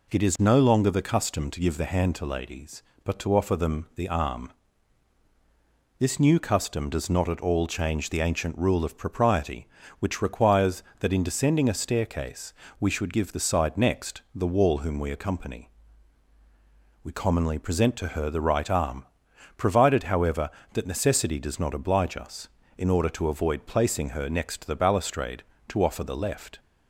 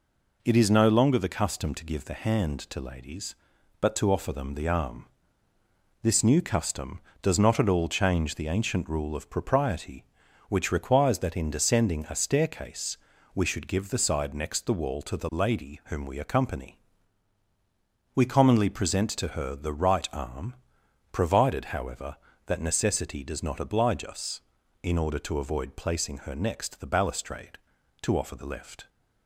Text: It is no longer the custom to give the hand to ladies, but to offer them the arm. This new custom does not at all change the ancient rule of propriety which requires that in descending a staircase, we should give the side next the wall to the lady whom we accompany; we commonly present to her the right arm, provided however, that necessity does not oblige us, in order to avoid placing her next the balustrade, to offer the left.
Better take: second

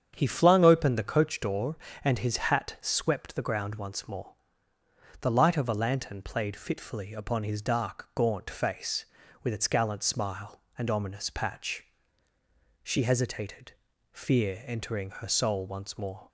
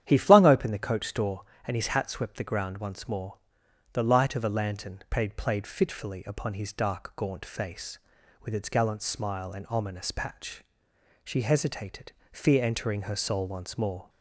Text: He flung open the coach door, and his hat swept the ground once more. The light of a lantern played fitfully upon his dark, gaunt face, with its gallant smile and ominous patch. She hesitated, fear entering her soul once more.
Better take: first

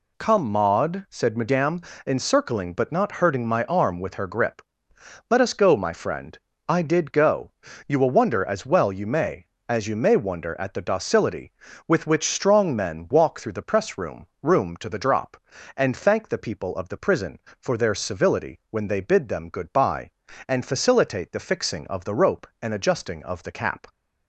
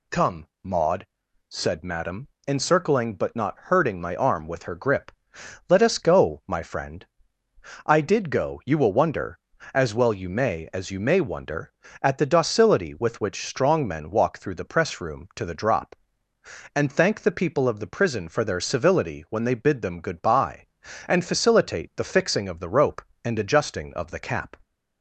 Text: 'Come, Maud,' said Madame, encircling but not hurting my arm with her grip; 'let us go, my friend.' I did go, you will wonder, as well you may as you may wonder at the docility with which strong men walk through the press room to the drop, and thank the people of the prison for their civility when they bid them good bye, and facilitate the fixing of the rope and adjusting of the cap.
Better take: second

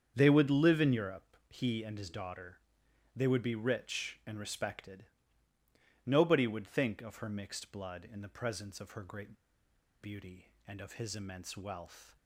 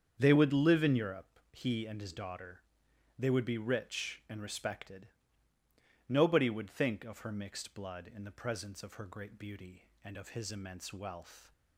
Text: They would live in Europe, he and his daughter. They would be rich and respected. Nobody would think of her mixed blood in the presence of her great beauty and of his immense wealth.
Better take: second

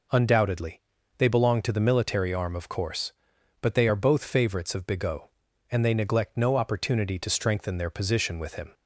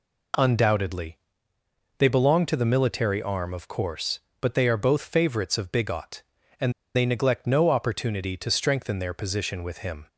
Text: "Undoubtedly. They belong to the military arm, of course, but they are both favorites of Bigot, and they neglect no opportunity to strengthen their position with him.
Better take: first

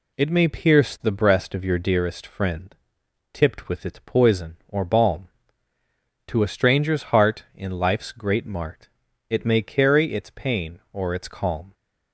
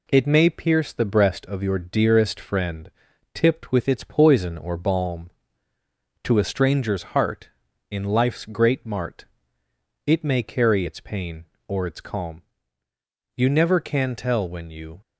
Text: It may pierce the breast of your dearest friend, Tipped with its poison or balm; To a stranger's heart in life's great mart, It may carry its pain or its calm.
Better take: first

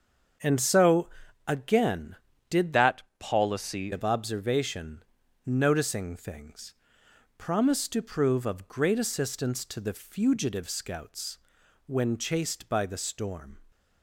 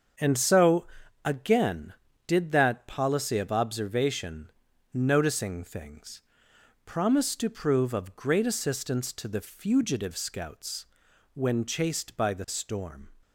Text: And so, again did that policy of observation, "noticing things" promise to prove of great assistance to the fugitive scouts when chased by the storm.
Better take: second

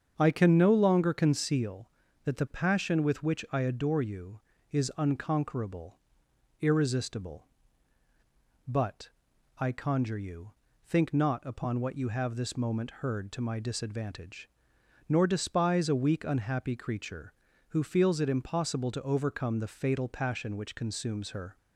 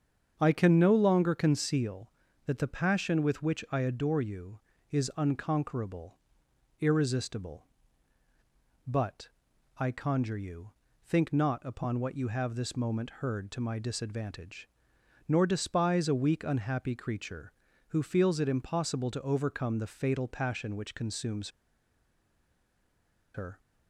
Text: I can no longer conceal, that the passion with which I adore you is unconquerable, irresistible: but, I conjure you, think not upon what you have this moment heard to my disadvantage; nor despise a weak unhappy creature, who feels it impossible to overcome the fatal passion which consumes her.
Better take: first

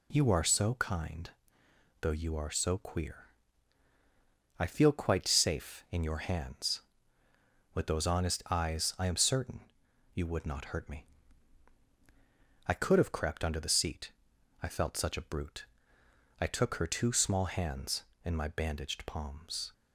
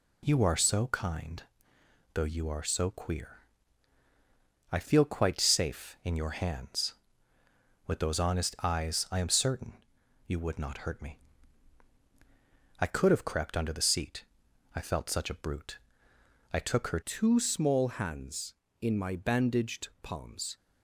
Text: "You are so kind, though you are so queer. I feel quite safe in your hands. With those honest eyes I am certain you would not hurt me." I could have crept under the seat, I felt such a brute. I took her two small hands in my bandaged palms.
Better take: first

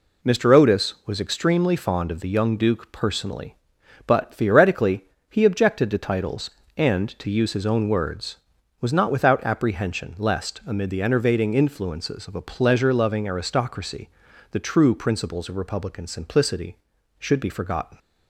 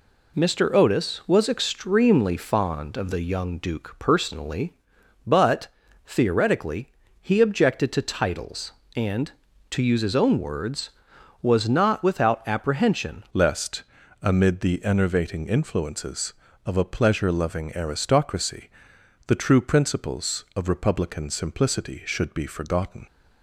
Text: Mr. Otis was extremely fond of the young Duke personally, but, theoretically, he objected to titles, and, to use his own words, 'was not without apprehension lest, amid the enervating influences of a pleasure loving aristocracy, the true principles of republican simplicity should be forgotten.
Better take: first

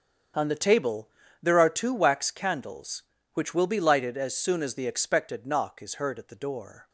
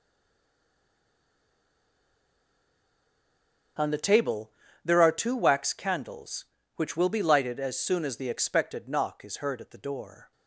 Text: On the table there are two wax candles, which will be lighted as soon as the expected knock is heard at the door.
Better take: first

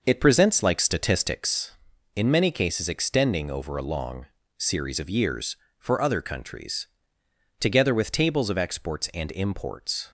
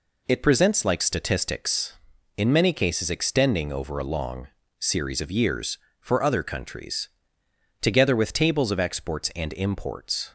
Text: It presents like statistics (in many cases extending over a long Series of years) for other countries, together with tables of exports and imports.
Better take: second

